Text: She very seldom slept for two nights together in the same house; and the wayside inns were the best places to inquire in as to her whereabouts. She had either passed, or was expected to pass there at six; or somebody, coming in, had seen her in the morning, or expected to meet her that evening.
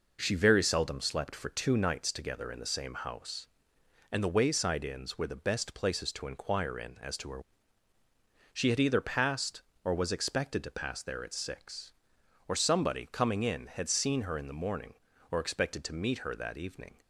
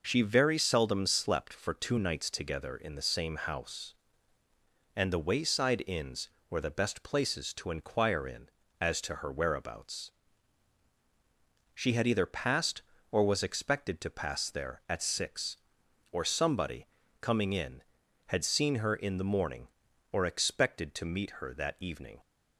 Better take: second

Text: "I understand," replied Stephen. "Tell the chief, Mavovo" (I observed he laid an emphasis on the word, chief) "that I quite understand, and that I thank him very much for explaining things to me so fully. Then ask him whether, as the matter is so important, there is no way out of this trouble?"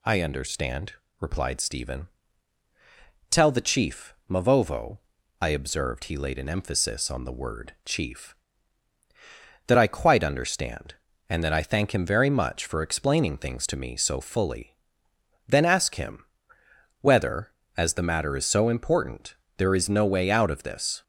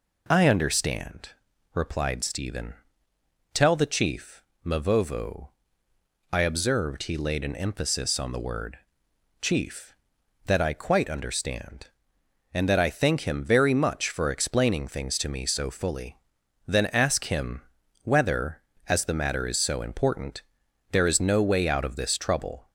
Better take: second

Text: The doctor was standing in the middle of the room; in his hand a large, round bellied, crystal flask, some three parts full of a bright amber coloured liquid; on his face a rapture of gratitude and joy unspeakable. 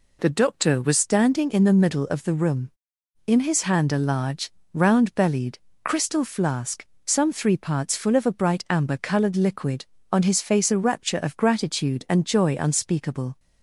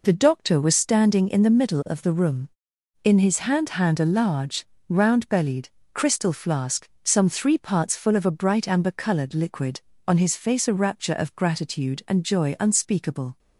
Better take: first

